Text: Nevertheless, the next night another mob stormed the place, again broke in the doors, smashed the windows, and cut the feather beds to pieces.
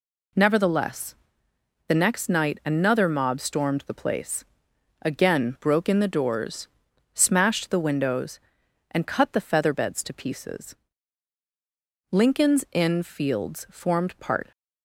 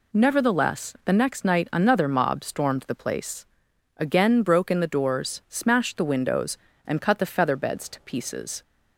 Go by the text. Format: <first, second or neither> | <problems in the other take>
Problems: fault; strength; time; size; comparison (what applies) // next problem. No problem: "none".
second | goes on to say "Lincoln's Inn Fields formed part"; strong; from 12.1 s on; 2.4 s long